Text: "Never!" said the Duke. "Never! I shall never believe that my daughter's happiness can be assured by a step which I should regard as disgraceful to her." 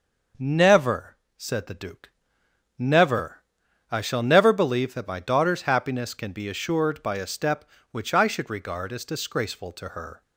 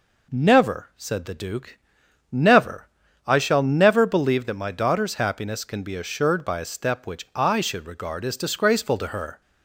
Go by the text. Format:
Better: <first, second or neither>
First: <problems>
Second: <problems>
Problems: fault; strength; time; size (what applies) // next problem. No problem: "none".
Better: neither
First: none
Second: none